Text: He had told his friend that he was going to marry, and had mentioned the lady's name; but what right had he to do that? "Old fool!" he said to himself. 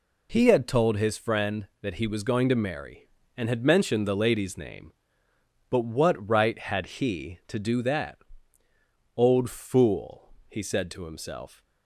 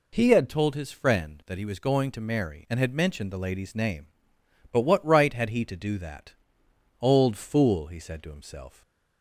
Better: first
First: none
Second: changes voice at "told"; from 0.4 s on; 8.4 s long // stays silent after the last word; slight; from 8.7 s on; 0.5 s long

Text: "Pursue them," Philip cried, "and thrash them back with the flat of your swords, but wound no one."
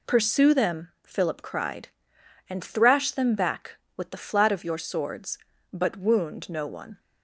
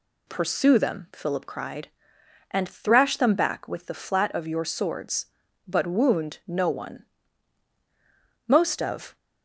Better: first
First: none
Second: goes on to say "Most of"; noticeable; from 8.4 s on; 0.70 s long

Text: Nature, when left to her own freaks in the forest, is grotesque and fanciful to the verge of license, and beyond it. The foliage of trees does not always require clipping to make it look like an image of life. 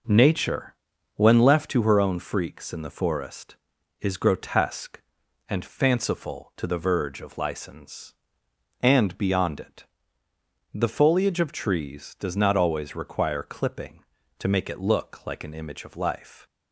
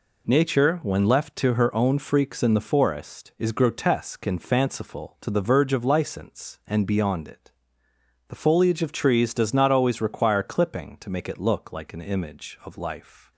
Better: second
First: starts louder than the rest; noticeable; until 1.8 s; 5 dB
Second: none

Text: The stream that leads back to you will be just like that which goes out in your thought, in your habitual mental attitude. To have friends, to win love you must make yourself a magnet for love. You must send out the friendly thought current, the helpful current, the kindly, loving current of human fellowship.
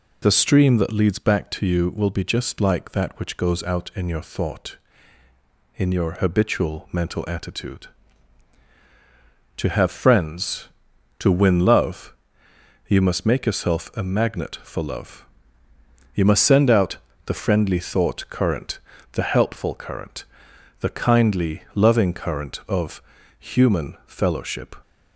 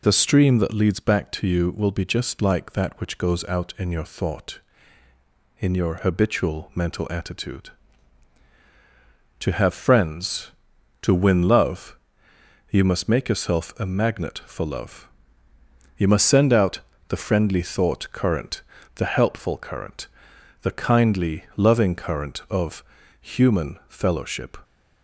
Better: neither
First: pauses between "love" and "you"; noticeable; at 12.1 s; 0.74 s long // pauses between "out" and "the"; slight; at 16.9 s; 0.28 s long // pauses between "of" and "human"; at 23.0 s; 0.38 s long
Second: pauses between "love" and "you"; noticeable; at 11.9 s; 0.74 s long // pauses between "out" and "the"; slight; at 16.8 s; 0.28 s long // pauses between "of" and "human"; at 22.8 s; 0.38 s long

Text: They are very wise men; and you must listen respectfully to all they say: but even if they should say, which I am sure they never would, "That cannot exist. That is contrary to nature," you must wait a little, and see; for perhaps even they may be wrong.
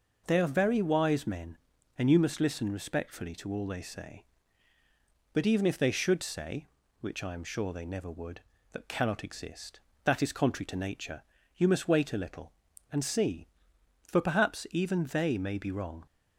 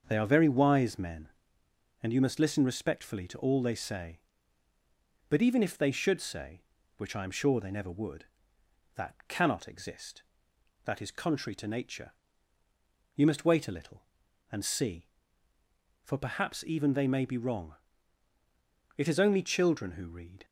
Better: first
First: none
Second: starts louder than the rest; until 1.0 s; 6.5 dB // goes on to say "It is only children who read"; from 18.9 s on; 1.4 s long

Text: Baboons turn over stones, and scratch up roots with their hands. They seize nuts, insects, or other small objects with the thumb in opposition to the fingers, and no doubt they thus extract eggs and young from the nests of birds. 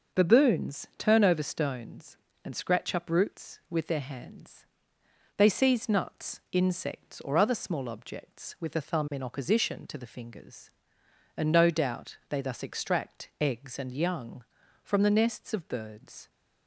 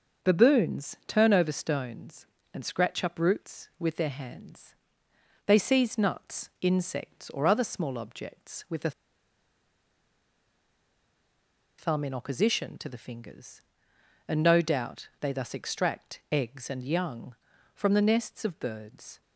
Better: first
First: starts louder than the rest; until 1.2 s; 6.5 dB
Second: starts louder than the rest; until 1.3 s; 6 dB // pauses between "the" and "thumb"; strong; at 8.9 s; 2.8 s long

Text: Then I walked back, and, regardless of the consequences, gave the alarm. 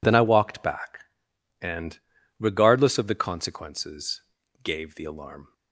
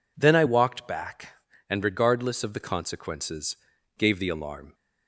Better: neither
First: none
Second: none

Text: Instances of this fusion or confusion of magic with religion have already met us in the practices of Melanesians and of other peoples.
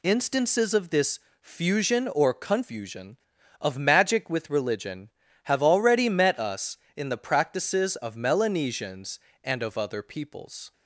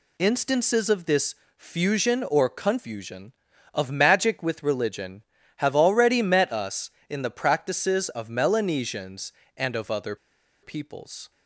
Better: first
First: pauses between "this" and "fusion"; slight; at 1.1 s; 0.22 s long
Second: pauses between "this" and "fusion"; slight; at 1.3 s; 0.22 s long // pauses between "other" and "peoples"; noticeable; at 10.1 s; 0.47 s long

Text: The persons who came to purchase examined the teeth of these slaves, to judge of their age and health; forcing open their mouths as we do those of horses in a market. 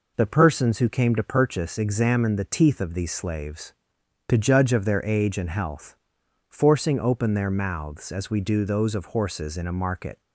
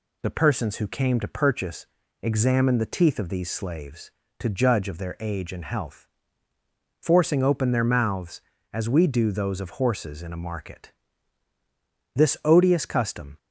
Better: first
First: none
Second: pauses between "purchase" and "examined"; slight; at 1.8 s; 0.36 s long // goes on to say "This odious custom"; noticeable; from 12.1 s on; 1.2 s long

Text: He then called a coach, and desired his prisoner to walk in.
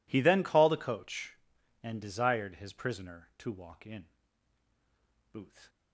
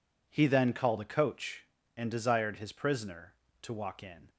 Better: second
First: goes on to say "Booth"; slight; from 5.3 s on; 0.36 s long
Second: none

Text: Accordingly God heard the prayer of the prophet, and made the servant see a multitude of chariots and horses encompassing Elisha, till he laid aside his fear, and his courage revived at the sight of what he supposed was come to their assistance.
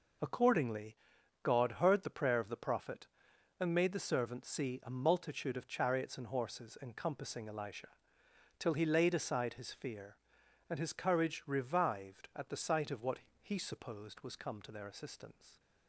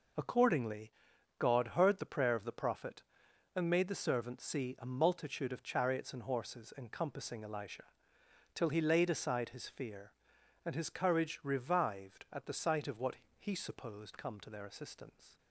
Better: first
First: pauses between "Accordingly" and "God"; noticeable; at 0.9 s; 0.46 s long // pauses between "what" and "he"; slight; at 13.1 s; 0.22 s long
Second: pauses between "Accordingly" and "God"; noticeable; at 0.9 s; 0.46 s long // pauses between "what" and "he"; slight; at 13.1 s; 0.22 s long // skips "was"; at 14.1 s

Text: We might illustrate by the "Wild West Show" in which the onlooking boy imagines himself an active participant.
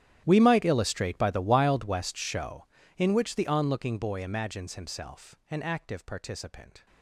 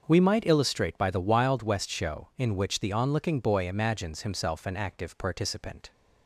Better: second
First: gets quieter; strong; throughout; 22.5 dB // starts louder than the rest; strong; until 1.2 s; 11.5 dB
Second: starts louder than the rest; until 1.0 s; 6.5 dB

